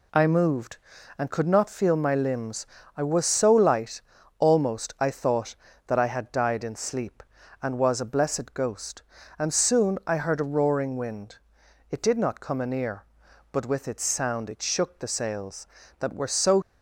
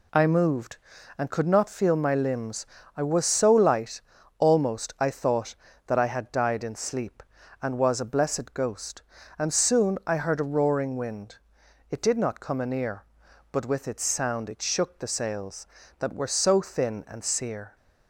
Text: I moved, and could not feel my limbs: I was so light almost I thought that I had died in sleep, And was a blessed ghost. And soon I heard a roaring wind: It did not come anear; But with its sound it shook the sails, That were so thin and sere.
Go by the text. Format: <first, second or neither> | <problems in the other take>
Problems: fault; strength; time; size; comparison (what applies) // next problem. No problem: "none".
second | pauses between "light" and "almost"; at 4.0 s; 0.38 s long; also in the second // stops before "thin and sere"; at 16.6 s